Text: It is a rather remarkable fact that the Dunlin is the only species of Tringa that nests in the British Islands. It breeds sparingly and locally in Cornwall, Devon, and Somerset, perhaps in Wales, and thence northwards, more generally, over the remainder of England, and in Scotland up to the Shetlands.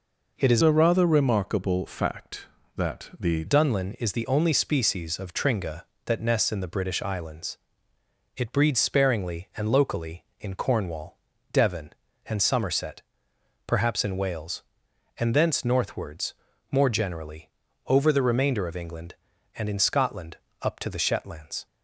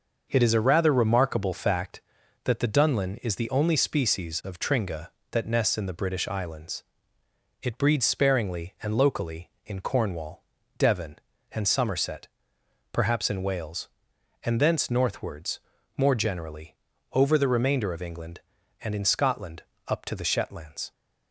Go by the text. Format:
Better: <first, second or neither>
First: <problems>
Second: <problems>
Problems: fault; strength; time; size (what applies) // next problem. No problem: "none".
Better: second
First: changes voice from "a" to "the"; from 0.6 to 3.4 s; 2.8 s long // pauses between "Scotland" and "up"; slight; at 20.3 s; 0.26 s long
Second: pauses between "Scotland" and "up"; slight; at 19.6 s; 0.26 s long